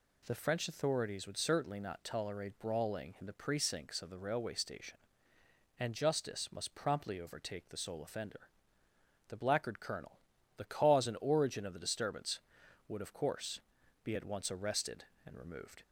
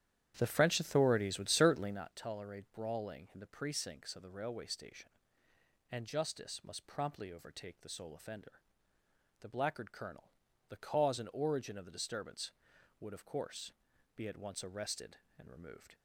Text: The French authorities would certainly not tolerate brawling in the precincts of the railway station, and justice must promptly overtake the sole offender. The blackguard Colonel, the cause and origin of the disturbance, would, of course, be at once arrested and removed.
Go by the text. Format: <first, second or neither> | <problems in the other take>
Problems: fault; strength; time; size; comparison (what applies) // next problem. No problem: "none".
first | starts louder than the rest; strong; until 2.1 s; 10.5 dB